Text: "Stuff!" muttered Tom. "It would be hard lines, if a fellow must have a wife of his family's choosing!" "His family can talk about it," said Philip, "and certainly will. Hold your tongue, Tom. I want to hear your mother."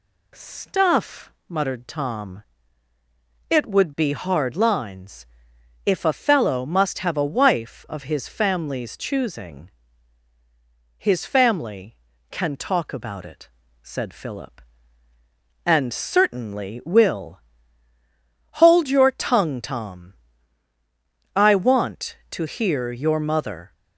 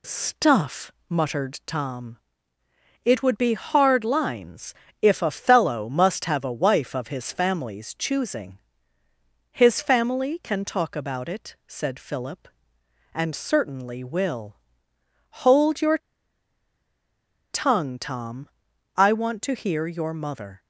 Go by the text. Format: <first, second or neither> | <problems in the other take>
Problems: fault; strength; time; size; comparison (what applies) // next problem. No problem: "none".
first | pauses between "your" and "tongue"; strong; at 15.9 s; 1.5 s long